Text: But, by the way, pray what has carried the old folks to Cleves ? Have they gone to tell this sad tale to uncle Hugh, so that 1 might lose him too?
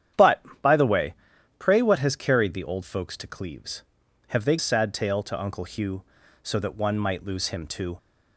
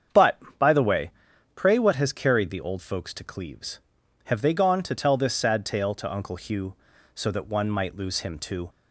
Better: second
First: starts louder than the rest; strong; until 1.8 s; 9.5 dB // skips "gone to tell this"; at 4.5 s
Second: starts louder than the rest; strong; until 1.7 s; 8 dB

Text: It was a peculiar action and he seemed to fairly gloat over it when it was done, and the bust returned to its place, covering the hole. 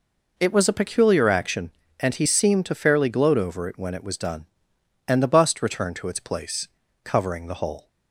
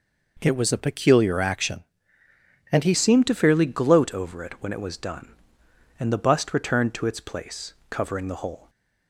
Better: first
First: none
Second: changes voice at "seemed"; from 2.9 s on; 5.7 s long

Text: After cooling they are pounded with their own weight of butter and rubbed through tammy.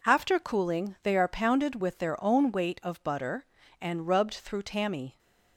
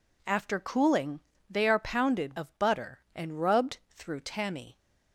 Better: first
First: none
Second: pauses between "cooling" and "they"; slight; at 1.1 s; 0.30 s long // skips "with their own weight"; at 2.3 s

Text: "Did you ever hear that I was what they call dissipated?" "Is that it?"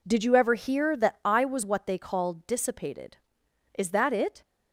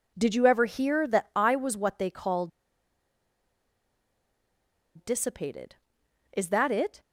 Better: first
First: none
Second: pauses between "call" and "dissipated"; strong; at 2.4 s; 2.4 s long

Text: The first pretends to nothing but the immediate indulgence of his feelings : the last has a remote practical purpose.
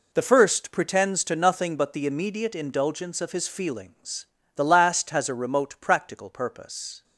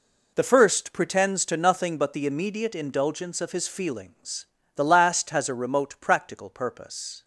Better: neither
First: none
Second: none

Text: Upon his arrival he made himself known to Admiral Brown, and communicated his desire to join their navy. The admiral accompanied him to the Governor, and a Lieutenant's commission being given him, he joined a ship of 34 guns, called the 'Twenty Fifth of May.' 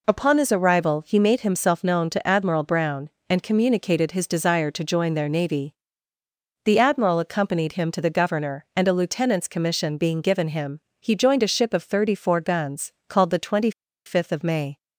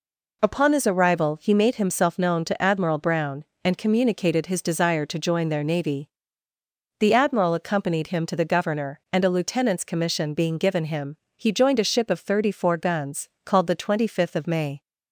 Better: second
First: pauses between "Twenty" and "Fifth"; slight; at 13.7 s; 0.35 s long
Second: none

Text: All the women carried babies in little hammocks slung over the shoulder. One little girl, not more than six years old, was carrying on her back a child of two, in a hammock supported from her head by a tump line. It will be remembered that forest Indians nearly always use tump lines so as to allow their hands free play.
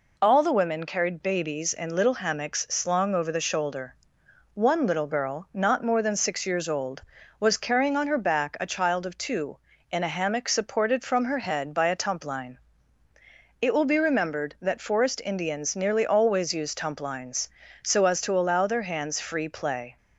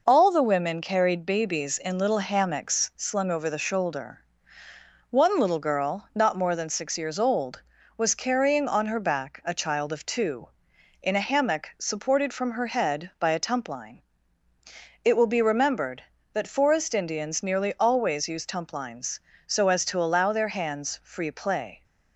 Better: neither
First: none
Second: none

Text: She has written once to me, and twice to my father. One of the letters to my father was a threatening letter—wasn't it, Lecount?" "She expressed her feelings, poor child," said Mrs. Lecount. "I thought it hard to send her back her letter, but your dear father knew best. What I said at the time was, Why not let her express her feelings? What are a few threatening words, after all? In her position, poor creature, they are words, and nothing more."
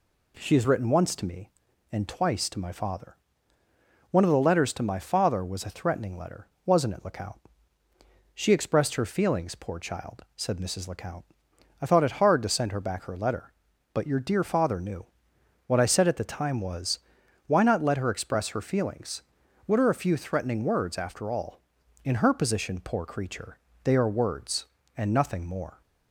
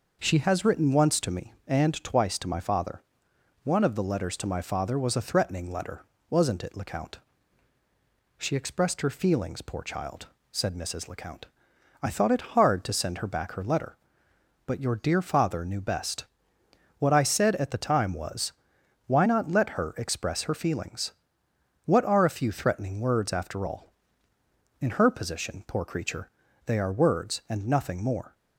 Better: second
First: skips "best"; at 15.3 s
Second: none

